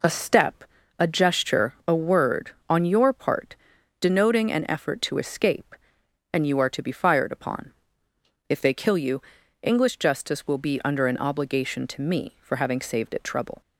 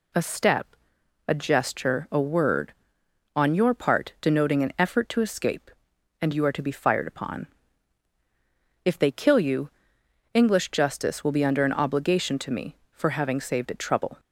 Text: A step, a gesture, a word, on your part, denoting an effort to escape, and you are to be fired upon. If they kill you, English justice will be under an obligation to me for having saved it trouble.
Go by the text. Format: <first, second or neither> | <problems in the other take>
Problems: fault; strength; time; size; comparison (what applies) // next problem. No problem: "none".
neither | none